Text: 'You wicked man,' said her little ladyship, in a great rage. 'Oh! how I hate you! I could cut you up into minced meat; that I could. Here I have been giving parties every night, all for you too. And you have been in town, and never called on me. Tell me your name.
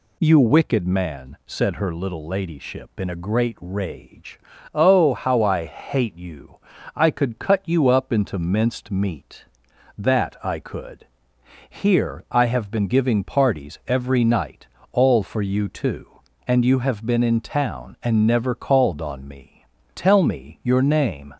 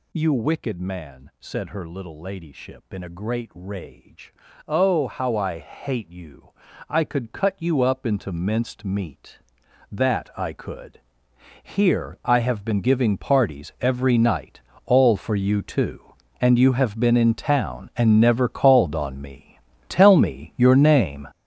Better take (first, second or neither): first